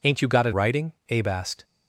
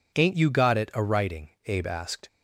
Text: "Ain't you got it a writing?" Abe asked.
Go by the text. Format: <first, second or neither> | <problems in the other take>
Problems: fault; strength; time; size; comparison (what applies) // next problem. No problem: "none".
second | skips "a"; at 0.5 s